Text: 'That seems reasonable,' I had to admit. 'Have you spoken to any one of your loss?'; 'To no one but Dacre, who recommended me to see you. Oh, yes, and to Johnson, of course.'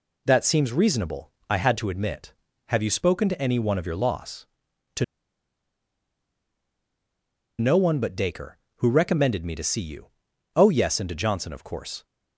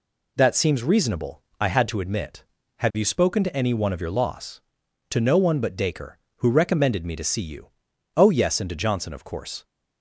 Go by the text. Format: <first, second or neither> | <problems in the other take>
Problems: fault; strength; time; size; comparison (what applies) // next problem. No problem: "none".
second | pauses between "To" and "no"; strong; at 5.0 s; 2.5 s long